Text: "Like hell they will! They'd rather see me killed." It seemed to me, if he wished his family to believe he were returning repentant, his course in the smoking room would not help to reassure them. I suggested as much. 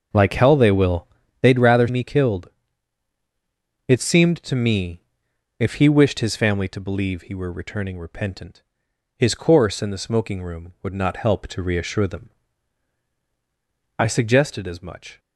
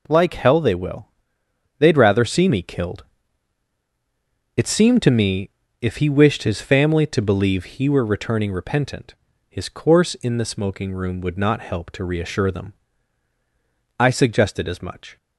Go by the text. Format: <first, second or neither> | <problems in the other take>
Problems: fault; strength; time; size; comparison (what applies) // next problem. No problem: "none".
second | starts louder than the rest; until 1.4 s; 6.5 dB // skips "see"; at 1.8 s